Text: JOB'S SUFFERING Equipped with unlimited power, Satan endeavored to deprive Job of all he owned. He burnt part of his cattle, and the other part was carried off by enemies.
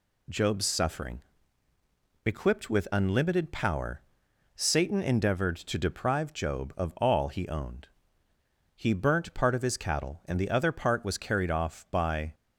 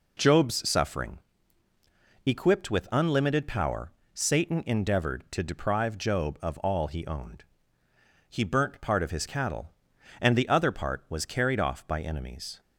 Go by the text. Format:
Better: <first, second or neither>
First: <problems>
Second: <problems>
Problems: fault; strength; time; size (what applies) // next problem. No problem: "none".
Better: second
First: pauses between "SUFFERING" and "Equipped"; at 1.2 s; 1.0 s long // stops before "enemies"; at 12.3 s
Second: pauses between "SUFFERING" and "Equipped"; at 1.1 s; 1.0 s long